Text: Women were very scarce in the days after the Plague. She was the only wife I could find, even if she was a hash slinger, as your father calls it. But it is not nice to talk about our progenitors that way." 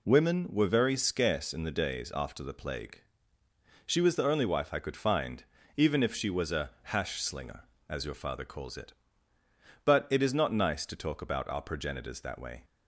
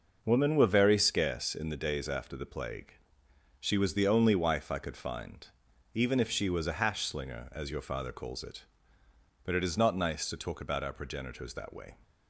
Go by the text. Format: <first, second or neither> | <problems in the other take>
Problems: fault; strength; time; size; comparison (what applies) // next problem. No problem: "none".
neither | none